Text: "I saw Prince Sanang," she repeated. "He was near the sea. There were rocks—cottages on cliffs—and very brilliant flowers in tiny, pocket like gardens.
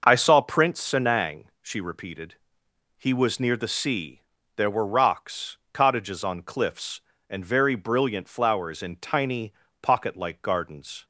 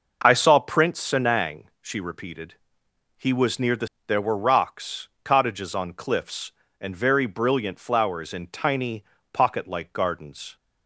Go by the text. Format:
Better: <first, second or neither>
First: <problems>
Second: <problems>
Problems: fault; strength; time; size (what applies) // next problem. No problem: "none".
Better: first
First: none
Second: skips "sea"; at 3.9 s